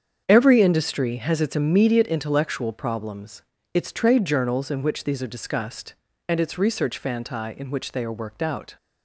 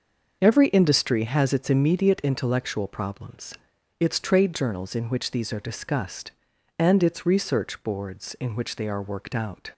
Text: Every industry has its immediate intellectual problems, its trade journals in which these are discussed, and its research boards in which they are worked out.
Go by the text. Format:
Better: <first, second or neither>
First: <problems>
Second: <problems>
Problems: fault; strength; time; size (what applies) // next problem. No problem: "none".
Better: second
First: starts louder than the rest; strong; until 1.2 s; 7.5 dB // says "fanti" for "boards"; at 6.9 s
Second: starts louder than the rest; until 1.4 s; 6 dB